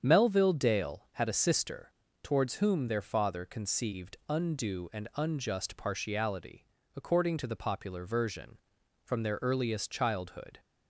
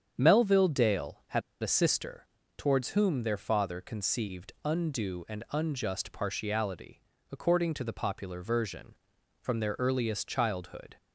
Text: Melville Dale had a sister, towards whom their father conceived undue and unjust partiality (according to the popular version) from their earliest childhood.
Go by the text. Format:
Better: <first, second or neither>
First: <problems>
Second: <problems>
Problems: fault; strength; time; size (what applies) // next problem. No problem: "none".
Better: first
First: starts louder than the rest; strong; until 1.0 s; 8 dB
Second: starts louder than the rest; strong; until 1.1 s; 8 dB // pauses between "had" and "a"; slight; at 1.4 s; 0.21 s long